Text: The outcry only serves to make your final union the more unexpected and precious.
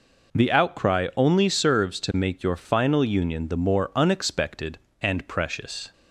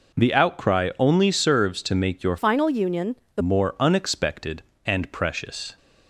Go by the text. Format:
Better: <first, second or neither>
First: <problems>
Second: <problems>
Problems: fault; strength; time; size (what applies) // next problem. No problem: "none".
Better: first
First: none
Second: changes voice from "final" to "the"; from 2.3 to 3.4 s; 1.1 s long // pauses between "union" and "the"; slight; at 3.1 s; 0.18 s long